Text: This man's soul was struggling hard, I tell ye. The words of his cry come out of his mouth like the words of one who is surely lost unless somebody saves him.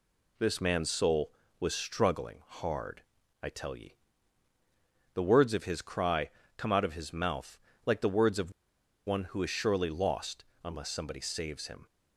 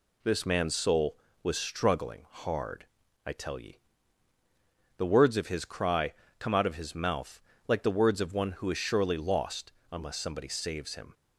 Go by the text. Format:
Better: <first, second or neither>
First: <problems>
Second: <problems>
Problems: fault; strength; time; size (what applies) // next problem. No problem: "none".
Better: second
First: pauses between "cry" and "come"; slight; at 6.2 s; 0.28 s long // pauses between "mouth" and "like"; slight; at 7.5 s; 0.28 s long // pauses between "of" and "one"; noticeable; at 8.5 s; 0.55 s long // pauses between "lost" and "unless"; slight; at 10.4 s; 0.20 s long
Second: pauses between "cry" and "come"; slight; at 6.1 s; 0.27 s long // pauses between "mouth" and "like"; slight; at 7.3 s; 0.28 s long // pauses between "lost" and "unless"; slight; at 9.7 s; 0.20 s long